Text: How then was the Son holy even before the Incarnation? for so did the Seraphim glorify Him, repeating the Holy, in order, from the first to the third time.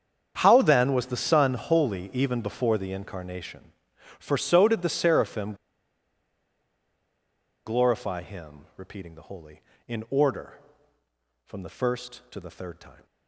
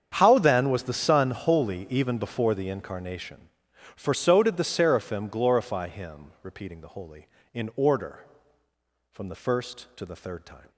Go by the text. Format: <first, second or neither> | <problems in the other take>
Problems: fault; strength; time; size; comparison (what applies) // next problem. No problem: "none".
second | starts louder than the rest; strong; until 1.3 s; 7.5 dB; strong in the second // pauses between "Seraphim" and "glorify"; strong; at 5.5 s; 2.1 s long